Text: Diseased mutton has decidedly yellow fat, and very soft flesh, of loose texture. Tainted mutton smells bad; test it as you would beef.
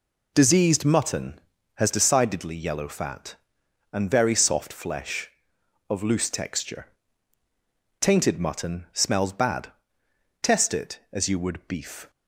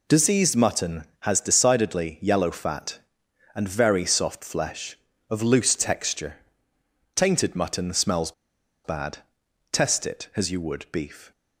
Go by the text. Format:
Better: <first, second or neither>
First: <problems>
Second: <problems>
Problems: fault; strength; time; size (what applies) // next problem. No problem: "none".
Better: first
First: none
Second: pauses between "smells" and "bad"; noticeable; at 8.3 s; 0.53 s long